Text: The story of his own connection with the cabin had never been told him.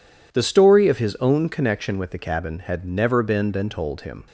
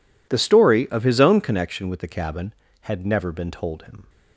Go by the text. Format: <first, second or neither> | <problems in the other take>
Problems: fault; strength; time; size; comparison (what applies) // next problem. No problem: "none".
second | says "been" twice; at 3.5 s